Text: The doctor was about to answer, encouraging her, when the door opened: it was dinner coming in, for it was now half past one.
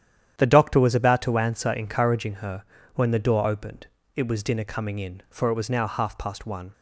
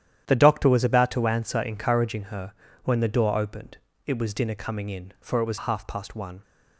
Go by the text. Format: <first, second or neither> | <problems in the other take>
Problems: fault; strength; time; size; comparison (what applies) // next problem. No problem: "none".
first | starts louder than the rest; strong; until 1.2 s; 10.5 dB; strong in the first // skips "now"; at 5.5 s